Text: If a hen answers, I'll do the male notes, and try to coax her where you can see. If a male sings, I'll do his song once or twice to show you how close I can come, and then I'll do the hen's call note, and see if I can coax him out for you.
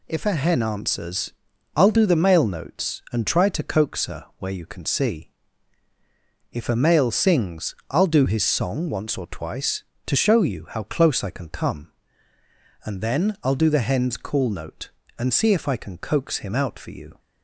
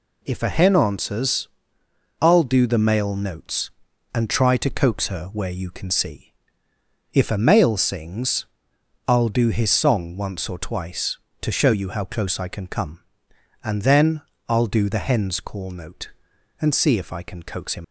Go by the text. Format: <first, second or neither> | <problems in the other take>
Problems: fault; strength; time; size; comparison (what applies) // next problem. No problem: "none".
first | pauses between "then" and "I'll"; slight; at 14.2 s; 0.26 s long // stops before "out for you"; at 17.8 s